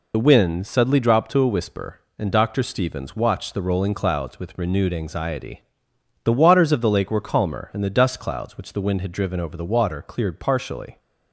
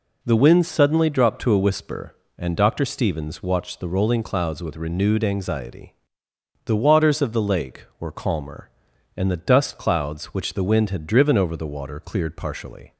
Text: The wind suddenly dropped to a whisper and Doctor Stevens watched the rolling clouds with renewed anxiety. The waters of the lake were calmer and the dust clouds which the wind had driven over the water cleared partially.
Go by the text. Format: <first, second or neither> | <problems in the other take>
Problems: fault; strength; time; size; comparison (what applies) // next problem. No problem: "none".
second | loses the start of "The"; at 0.1 s; 40 ms